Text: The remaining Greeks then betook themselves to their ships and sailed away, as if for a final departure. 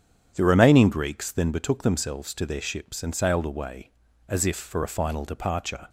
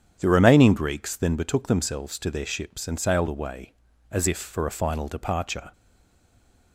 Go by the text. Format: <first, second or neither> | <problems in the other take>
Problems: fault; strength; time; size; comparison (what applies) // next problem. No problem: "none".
first | starts louder than the rest; strong; until 1.2 s; 9 dB; strong in the first // stays silent after the last word; from 5.7 s on; 1.0 s long